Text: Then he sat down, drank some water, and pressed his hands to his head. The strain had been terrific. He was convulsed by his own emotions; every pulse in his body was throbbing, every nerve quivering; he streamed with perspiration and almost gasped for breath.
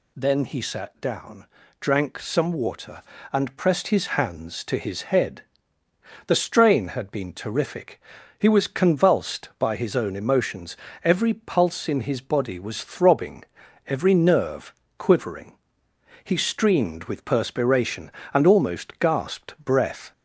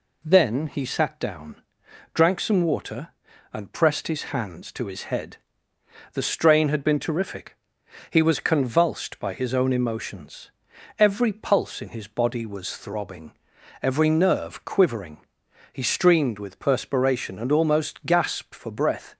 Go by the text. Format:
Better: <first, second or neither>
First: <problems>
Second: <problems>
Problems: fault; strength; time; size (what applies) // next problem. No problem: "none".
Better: second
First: pauses between "nerve" and "quivering"; slight; at 14.7 s; 0.24 s long // skips "for"; at 19.5 s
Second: none